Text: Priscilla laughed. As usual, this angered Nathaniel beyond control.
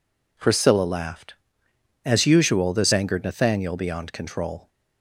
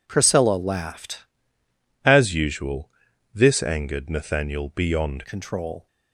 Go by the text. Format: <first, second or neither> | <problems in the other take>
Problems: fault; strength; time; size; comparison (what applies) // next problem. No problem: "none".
first | changes voice from "As" to "beyond"; from 2.0 to 5.2 s; 3.2 s long